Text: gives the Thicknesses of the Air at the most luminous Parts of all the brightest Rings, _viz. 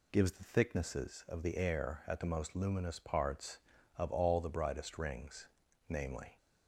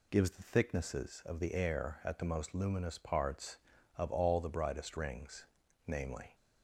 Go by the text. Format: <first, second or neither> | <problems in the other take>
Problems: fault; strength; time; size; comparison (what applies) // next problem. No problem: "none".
neither | none